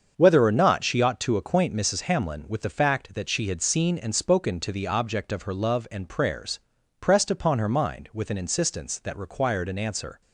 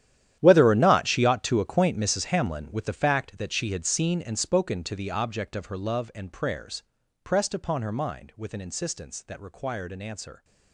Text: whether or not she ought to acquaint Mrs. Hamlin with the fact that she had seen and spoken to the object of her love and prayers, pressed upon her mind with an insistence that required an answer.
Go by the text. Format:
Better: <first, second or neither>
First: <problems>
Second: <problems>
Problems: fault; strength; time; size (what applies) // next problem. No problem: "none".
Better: first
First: starts louder than the rest; until 1.1 s; 7 dB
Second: gets quieter; strong; throughout; 16 dB // starts louder than the rest; strong; until 1.4 s; 11 dB